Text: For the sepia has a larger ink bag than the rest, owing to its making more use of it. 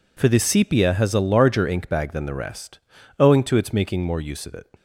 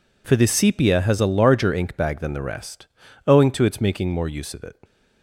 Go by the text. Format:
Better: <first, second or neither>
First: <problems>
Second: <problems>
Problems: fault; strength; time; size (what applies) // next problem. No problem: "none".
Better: neither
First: none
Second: none